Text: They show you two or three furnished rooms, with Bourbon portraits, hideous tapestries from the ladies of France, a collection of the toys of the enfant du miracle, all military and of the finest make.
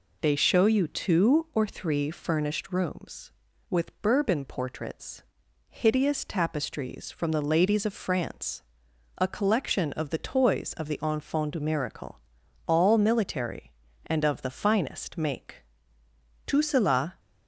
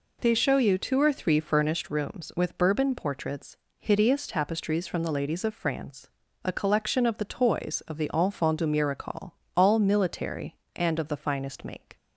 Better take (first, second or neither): second